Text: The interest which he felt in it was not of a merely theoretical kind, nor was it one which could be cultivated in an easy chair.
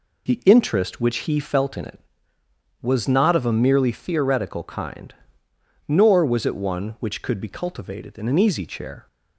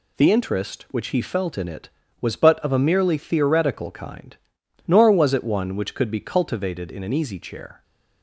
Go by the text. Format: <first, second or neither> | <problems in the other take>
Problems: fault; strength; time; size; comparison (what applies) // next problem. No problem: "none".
first | says "but" for "not"; at 2.3 s